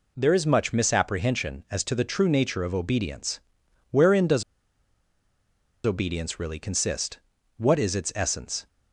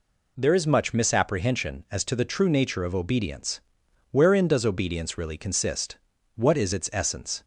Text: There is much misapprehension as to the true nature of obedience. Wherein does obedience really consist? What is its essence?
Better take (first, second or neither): second